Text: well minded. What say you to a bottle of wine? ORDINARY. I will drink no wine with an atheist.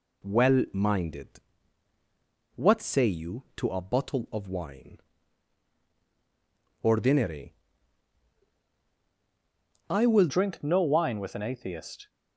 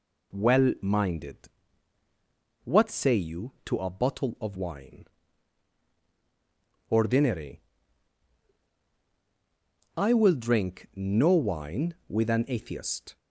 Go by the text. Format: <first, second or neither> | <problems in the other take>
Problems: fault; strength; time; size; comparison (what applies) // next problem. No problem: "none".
second | changes voice at "drink"; from 10.2 s on; 1.8 s long